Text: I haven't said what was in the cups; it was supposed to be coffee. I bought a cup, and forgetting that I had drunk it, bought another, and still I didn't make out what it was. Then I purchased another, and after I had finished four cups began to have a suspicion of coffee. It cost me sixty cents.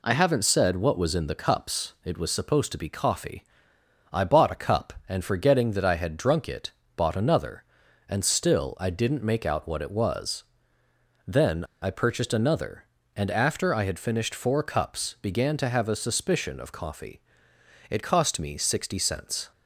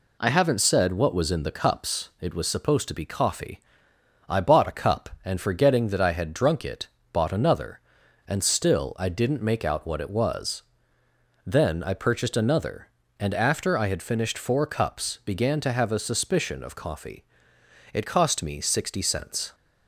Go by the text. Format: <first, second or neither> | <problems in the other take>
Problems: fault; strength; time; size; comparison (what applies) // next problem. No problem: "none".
second | pauses between "Then" and "I"; slight; at 11.6 s; 0.18 s long